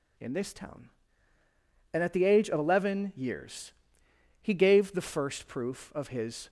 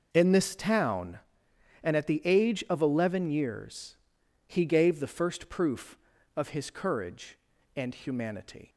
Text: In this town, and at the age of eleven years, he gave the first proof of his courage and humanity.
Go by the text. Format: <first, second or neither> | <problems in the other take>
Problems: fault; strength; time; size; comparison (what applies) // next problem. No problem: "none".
second | stops before "courage and humanity"; at 6.4 s